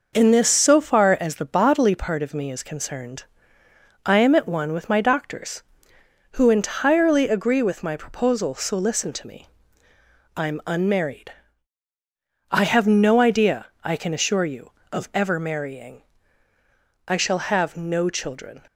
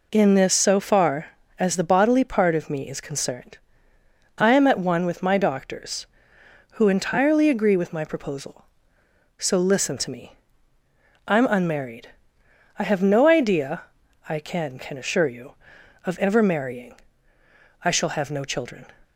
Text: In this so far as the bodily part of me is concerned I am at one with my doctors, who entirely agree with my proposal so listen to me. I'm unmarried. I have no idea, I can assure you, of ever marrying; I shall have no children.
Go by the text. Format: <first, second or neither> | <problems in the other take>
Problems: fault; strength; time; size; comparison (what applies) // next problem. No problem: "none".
first | pauses between "concerned" and "I"; noticeable; at 3.5 s; 0.80 s long; noticeable in the first // says "can" twice; at 14.7 s